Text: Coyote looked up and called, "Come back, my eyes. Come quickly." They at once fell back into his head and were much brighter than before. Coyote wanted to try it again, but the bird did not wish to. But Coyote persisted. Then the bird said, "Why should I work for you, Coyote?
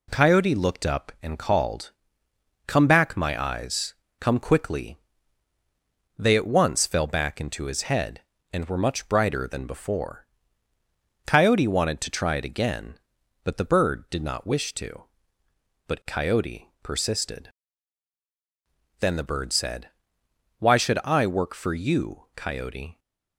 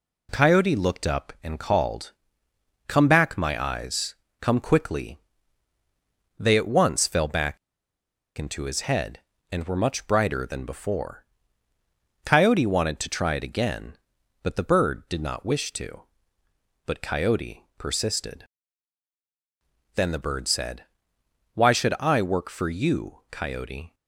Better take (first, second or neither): first